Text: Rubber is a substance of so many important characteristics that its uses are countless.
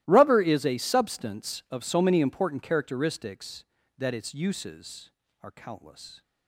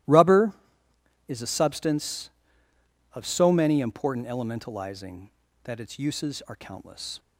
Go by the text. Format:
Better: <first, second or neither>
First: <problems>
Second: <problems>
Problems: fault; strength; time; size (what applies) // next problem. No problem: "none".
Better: first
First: starts louder than the rest; strong; until 1.0 s; 16.5 dB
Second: starts louder than the rest; strong; until 1.8 s; 15.5 dB // says "elementalizing" for "characteristics"; at 4.2 s